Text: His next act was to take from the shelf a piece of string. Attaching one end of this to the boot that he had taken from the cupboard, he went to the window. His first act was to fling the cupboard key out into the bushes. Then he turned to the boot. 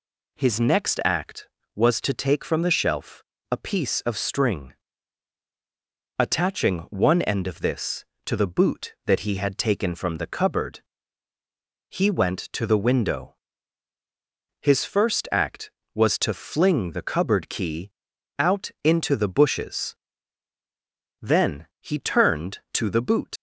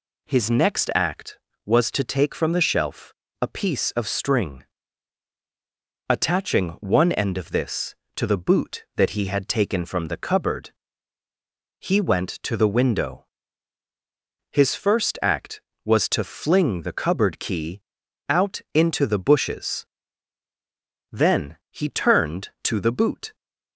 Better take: second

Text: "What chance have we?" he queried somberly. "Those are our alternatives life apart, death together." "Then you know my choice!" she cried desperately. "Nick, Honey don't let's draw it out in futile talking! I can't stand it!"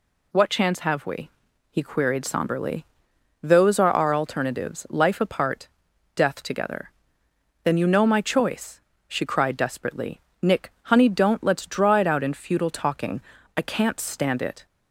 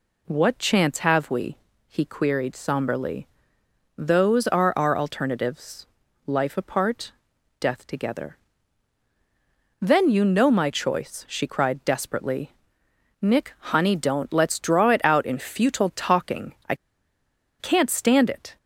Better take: first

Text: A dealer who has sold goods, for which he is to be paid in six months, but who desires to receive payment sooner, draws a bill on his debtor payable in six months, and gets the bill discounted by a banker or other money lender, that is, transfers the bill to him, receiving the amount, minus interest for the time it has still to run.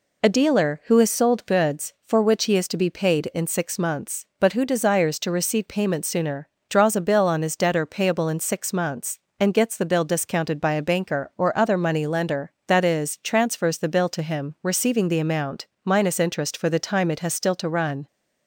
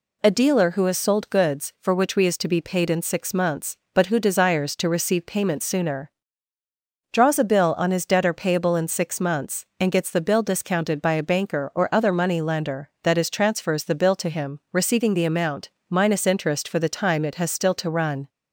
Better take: first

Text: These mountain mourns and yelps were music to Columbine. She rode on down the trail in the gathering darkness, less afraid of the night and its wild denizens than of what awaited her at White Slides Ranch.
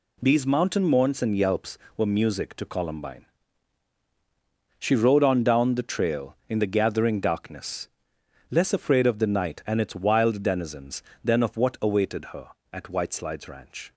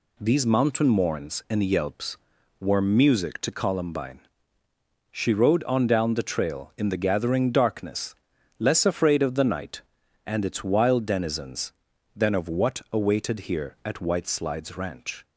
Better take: first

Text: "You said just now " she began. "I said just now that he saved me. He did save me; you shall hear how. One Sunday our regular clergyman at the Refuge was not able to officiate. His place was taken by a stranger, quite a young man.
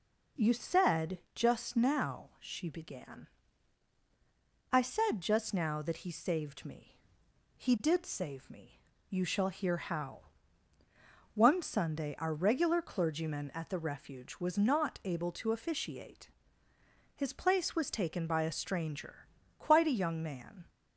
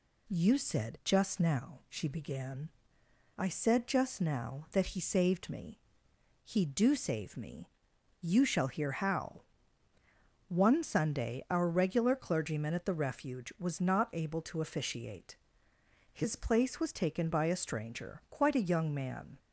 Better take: first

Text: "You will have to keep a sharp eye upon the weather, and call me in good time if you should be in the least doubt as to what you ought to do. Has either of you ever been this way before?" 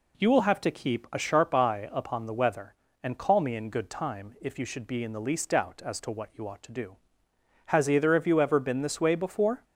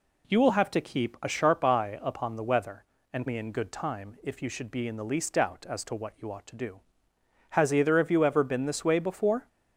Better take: first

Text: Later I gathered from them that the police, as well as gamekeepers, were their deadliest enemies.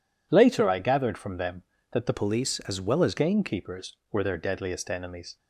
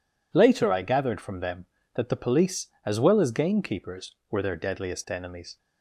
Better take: second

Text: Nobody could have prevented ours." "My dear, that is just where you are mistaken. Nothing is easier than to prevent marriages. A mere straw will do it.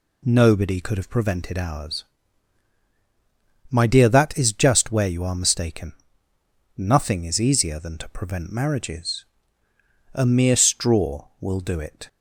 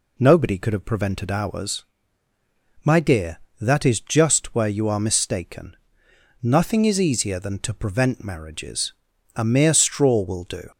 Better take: first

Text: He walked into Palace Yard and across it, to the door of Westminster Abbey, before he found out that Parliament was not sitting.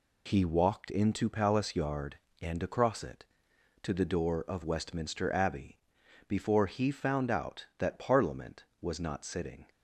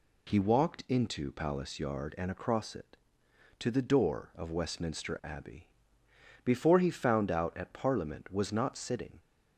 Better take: first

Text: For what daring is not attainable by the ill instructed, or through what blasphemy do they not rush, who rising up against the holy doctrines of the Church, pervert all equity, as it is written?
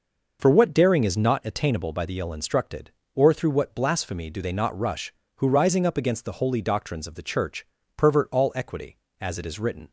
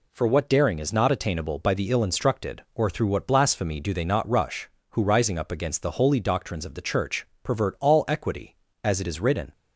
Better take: neither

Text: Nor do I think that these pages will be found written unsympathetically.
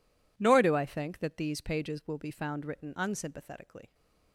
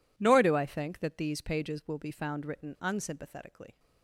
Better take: neither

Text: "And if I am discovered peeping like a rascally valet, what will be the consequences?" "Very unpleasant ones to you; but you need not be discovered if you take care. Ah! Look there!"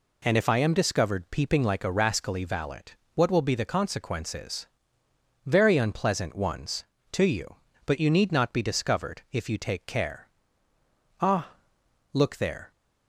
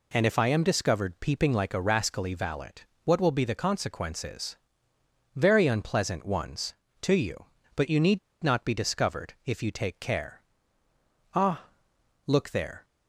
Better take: first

